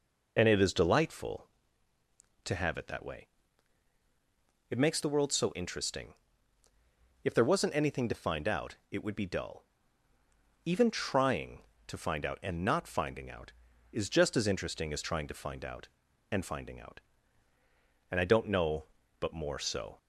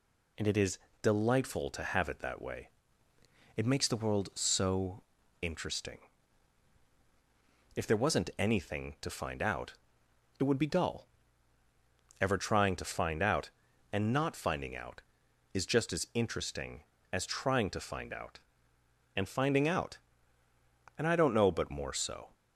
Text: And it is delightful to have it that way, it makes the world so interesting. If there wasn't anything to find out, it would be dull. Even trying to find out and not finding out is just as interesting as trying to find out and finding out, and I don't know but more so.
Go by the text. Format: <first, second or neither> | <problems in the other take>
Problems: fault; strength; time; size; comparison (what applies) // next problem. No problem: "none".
first | pauses between "is" and "delightful"; slight; at 0.7 s; 0.24 s long // pauses between "so" and "interesting"; at 5.0 s; 0.40 s long // says "Ever" for "Even"; at 12.2 s